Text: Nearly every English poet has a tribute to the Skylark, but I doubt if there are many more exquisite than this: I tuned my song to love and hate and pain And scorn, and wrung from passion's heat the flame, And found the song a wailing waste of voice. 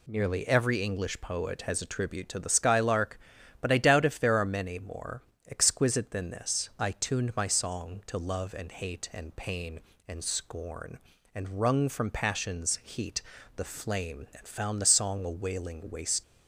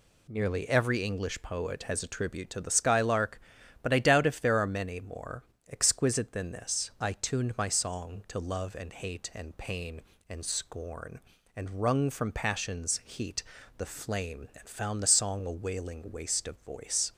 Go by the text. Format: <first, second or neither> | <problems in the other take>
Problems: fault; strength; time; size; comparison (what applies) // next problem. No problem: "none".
second | pauses between "more" and "exquisite"; slight; at 5.2 s; 0.28 s long; slight in the second // pauses between "heat" and "the"; slight; at 13.2 s; 0.36 s long; slight in the second // stops before "of voice"; at 16.2 s